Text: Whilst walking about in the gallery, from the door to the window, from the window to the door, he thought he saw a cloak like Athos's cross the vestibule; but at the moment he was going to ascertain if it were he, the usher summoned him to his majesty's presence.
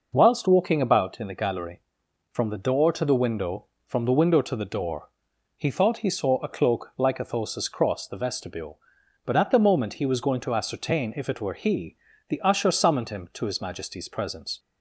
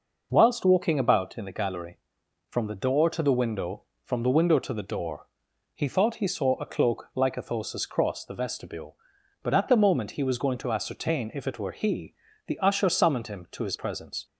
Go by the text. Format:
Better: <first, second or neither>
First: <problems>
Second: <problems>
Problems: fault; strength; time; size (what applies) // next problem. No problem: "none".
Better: first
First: none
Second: skips "majesty's"; at 13.7 s